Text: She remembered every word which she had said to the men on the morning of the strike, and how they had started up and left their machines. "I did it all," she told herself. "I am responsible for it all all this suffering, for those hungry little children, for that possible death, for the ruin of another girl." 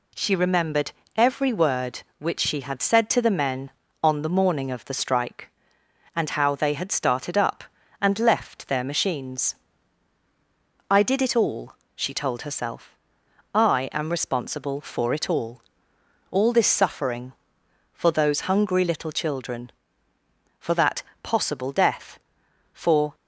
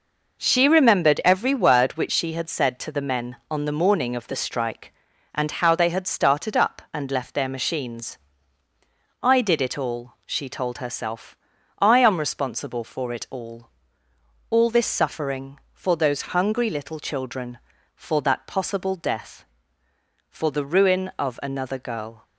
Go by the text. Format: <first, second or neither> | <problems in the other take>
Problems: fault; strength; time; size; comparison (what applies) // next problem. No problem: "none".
second | pauses between "remembered" and "every"; slight; at 0.9 s; 0.24 s long // pauses between "all" and "all"; noticeable; at 15.6 s; 0.70 s long; noticeable in the second // pauses between "that" and "possible"; slight; at 21.0 s; 0.20 s long // stops before "the ruin of another girl"; at 23.1 s